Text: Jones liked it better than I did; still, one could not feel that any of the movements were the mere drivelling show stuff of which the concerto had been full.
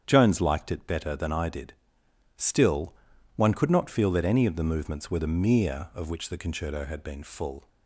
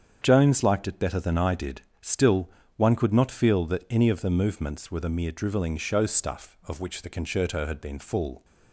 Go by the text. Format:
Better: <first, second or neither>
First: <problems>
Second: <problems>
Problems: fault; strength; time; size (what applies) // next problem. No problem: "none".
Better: second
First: starts louder than the rest; strong; until 1.0 s; 8 dB // skips "drivelling show stuff"; at 5.9 s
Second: starts louder than the rest; strong; until 1.2 s; 7.5 dB